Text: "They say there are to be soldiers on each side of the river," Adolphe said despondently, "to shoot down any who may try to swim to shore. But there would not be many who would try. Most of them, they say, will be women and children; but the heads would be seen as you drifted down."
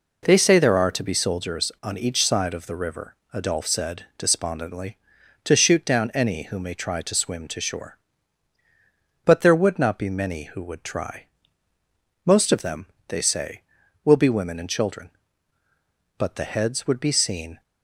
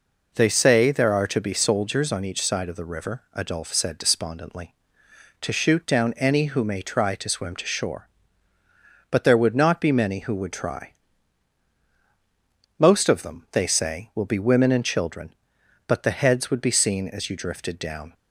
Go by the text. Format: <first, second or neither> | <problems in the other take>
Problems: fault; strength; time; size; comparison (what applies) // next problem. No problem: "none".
second | stops before "as you drifted down"; at 17.6 s